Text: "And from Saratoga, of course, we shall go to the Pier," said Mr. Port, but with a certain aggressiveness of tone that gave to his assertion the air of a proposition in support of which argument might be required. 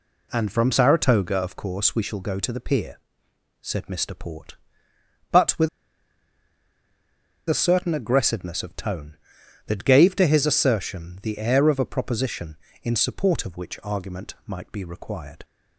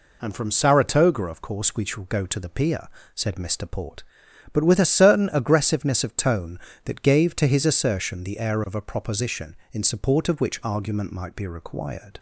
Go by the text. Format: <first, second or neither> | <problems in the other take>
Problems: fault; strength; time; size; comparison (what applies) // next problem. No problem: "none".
second | pauses between "with" and "a"; strong; at 5.6 s; 1.8 s long